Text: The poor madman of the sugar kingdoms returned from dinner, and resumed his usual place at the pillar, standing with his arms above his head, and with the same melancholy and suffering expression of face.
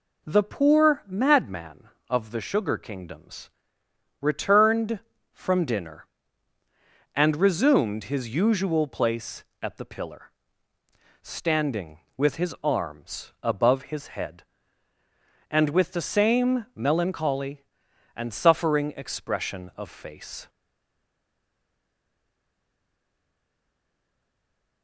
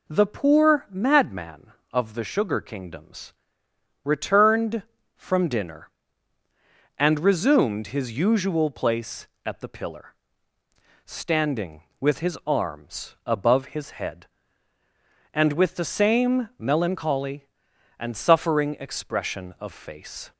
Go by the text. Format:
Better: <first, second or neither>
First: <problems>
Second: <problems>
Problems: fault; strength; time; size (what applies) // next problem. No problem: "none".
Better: second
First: pauses between "kingdoms" and "returned"; noticeable; at 3.4 s; 0.72 s long // stays silent after the last word; strong; from 20.4 s on; 4.4 s long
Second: pauses between "kingdoms" and "returned"; noticeable; at 3.3 s; 0.72 s long